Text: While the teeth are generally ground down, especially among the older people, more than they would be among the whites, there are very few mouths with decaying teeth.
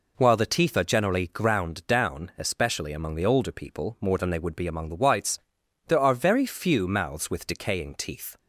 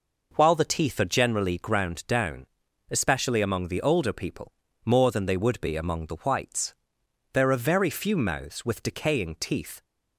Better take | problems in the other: neither | none

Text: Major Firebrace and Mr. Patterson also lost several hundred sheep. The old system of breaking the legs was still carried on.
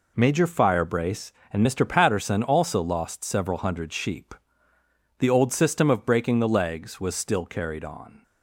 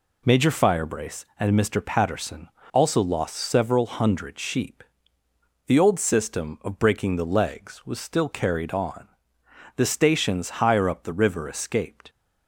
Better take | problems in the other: first | pauses between "Patterson" and "also"; slight; at 2.4 s; 0.26 s long // goes on to say "The stations higher up the river escaped"; strong; from 9.7 s on; 2.3 s long

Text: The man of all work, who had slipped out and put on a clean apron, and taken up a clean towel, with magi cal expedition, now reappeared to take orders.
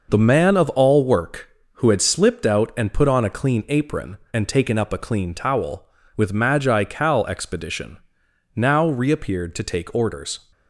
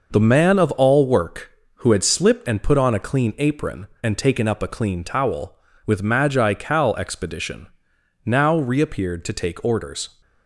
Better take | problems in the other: first | skips "out"; at 2.4 s

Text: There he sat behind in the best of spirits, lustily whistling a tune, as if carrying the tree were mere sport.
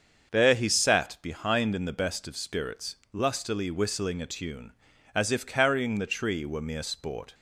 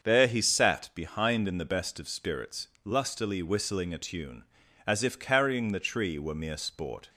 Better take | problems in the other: neither | starts louder than the rest; the same in both

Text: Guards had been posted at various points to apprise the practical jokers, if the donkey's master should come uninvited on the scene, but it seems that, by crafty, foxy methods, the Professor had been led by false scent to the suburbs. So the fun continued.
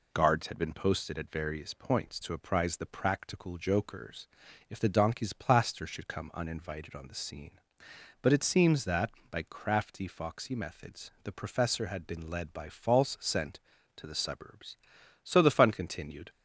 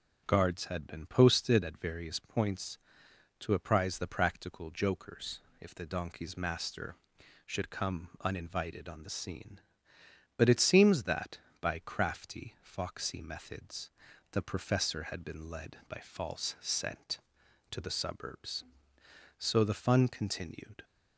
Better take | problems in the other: second | says "plaster" for "master"; at 5.3 s

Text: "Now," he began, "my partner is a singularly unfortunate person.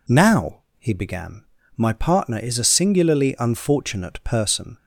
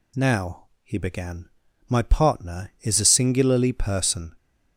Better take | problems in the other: first | skips "unfortunate"; at 3.7 s

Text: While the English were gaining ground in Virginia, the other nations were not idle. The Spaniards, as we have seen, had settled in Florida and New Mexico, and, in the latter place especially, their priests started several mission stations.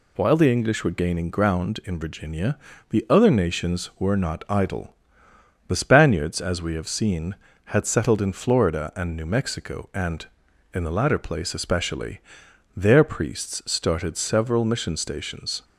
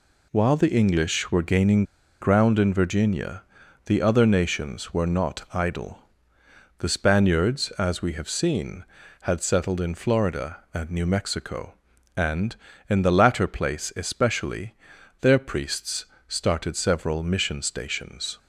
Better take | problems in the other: first | pauses between "gaining" and "ground"; at 1.8 s; 0.36 s long // pauses between "priests" and "started"; slight; at 16.0 s; 0.22 s long

